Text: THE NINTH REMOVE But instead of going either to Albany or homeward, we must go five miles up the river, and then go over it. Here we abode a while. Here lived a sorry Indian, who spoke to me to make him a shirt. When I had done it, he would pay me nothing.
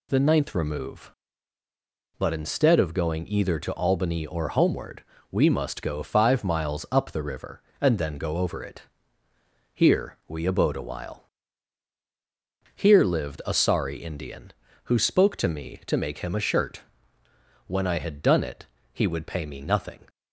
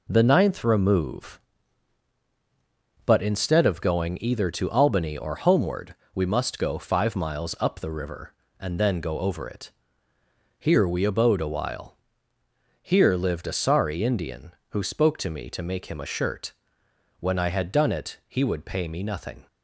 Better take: neither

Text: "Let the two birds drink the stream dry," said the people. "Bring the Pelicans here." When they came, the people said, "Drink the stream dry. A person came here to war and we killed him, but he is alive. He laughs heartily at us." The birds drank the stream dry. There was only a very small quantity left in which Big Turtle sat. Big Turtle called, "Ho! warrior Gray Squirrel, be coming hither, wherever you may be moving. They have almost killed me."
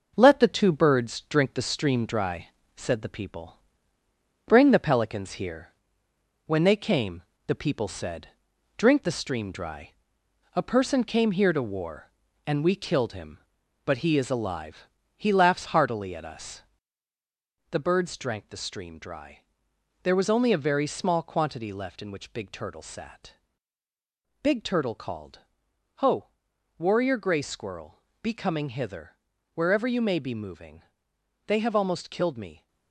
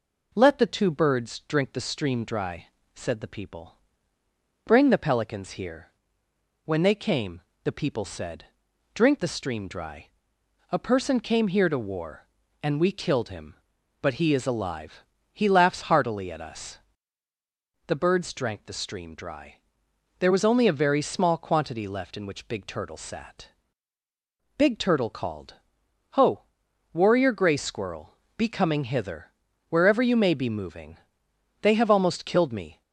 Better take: second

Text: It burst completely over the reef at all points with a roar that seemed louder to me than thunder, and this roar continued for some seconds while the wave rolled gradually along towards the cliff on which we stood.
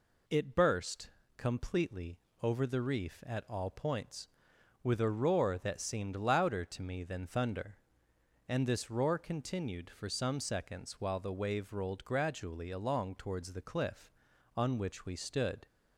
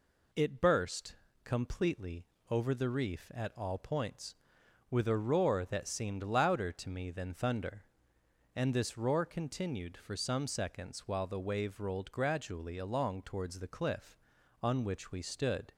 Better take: neither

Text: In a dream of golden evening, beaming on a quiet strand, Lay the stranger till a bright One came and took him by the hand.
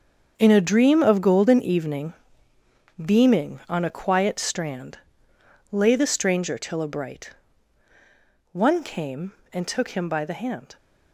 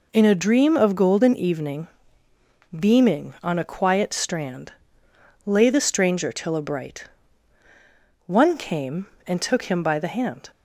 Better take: second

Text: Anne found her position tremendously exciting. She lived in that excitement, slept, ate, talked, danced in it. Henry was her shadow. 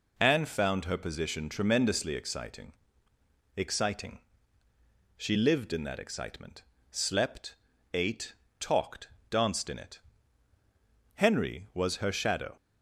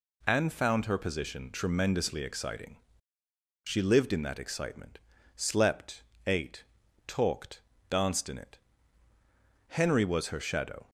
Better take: second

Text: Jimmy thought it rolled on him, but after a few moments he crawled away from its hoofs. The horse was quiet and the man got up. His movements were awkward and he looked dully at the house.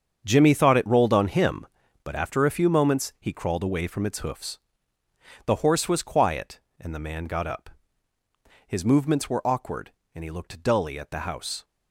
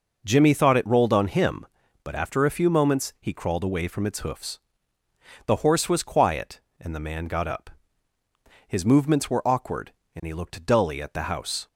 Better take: second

